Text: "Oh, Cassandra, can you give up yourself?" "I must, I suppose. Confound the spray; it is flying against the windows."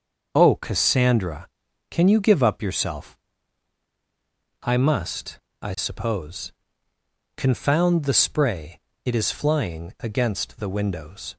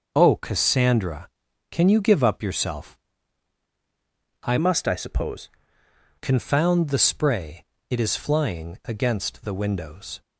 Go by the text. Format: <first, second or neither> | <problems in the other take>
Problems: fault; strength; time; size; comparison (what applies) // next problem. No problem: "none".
first | starts louder than the rest; noticeable; until 1.1 s; 6 dB; also in the first // changes voice from "must" to "suppose"; from 4.5 to 5.5 s; 1.0 s long